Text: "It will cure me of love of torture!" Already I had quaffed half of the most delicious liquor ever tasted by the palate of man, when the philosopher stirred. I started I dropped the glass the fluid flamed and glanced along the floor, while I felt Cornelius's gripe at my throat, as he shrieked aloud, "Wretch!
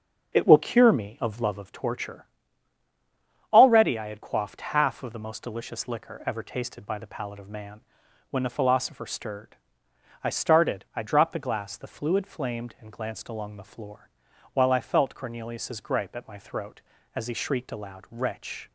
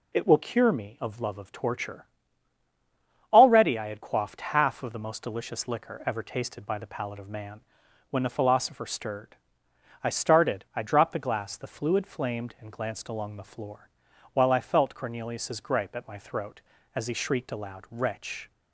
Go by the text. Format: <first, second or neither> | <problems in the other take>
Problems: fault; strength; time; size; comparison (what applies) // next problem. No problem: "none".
second | starts louder than the rest; until 1.8 s; 6.5 dB